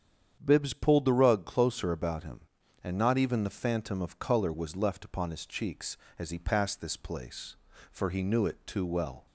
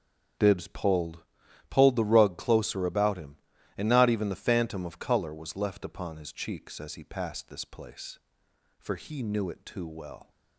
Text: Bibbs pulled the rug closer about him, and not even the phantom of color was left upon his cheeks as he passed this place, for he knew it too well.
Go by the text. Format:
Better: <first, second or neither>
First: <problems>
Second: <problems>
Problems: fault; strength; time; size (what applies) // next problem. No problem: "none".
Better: first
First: starts louder than the rest; strong; until 1.4 s; 8.5 dB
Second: starts louder than the rest; strong; until 1.8 s; 8 dB // says "pulled" twice; at 1.7 s